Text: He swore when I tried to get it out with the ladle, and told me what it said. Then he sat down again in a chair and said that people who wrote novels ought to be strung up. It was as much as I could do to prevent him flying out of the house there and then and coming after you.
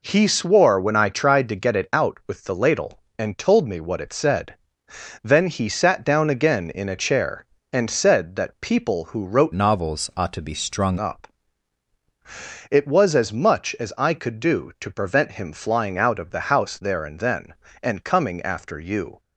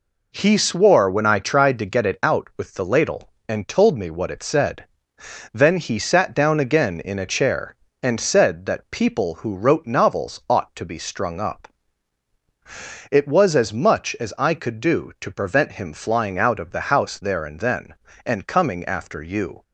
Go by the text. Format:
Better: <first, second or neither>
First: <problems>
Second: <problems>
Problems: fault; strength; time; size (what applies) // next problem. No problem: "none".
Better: second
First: changes voice from "novels" to "strung"; from 9.5 to 10.9 s; 1.4 s long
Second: none